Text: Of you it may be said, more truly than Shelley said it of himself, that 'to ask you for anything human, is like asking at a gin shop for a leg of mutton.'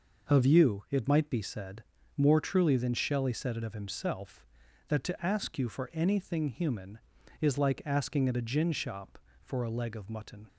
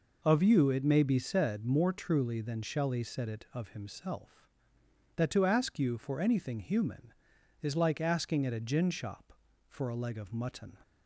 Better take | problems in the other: second | says "might" for "may"; at 1.0 s

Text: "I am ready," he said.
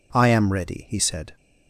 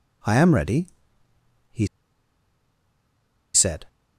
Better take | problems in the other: first | pauses between "he" and "said"; strong; at 1.8 s; 1.6 s long

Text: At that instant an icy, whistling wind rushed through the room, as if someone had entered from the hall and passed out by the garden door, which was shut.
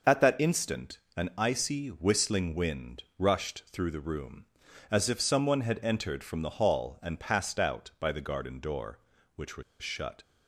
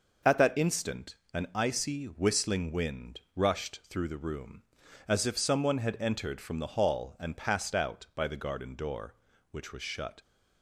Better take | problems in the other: second | pauses between "instant" and "an"; slight; at 0.9 s; 0.18 s long; slight in the second // pauses between "was" and "shut"; slight; at 9.6 s; 0.18 s long

